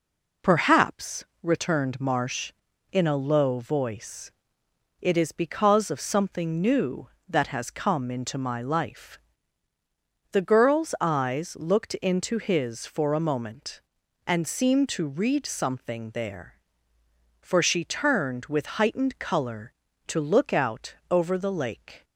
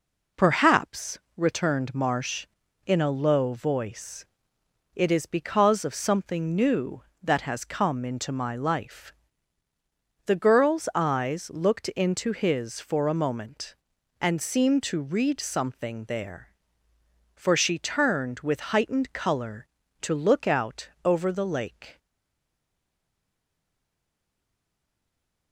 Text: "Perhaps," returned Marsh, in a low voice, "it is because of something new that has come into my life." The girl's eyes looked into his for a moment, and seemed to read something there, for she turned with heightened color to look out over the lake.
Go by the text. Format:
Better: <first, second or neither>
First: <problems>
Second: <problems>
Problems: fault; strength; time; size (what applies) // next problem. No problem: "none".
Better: first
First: pauses between "out" and "over"; slight; at 20.9 s; 0.16 s long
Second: pauses between "out" and "over"; slight; at 20.8 s; 0.16 s long // stays silent after the last word; strong; from 21.9 s on; 3.6 s long